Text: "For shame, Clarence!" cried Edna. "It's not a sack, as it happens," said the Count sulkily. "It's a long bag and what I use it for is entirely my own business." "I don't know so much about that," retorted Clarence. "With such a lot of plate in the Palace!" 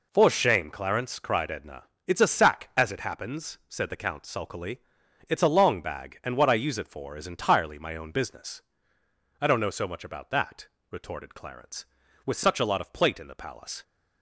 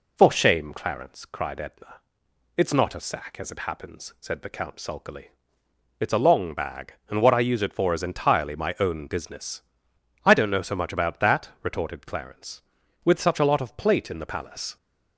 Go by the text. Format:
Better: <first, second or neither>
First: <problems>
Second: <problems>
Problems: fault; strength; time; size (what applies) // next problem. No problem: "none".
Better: second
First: skips "not"; at 2.2 s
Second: none